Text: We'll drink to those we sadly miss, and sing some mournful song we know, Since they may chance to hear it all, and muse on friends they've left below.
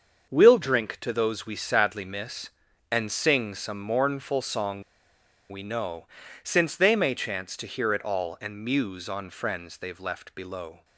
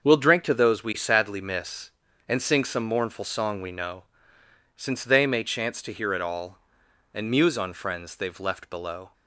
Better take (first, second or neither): second